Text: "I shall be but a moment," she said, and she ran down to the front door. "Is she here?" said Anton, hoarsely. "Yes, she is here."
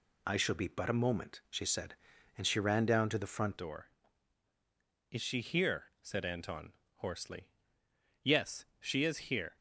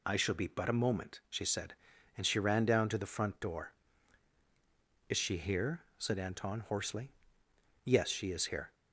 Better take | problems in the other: second | changes voice at "door"; from 3.5 s on; 6.0 s long

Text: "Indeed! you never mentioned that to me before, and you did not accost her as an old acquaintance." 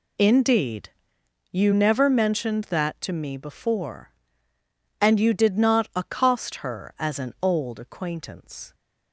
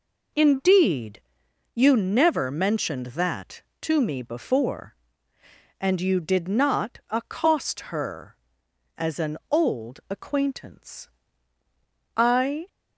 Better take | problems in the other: first | goes on to say "I"; from 12.1 s on; 0.52 s long

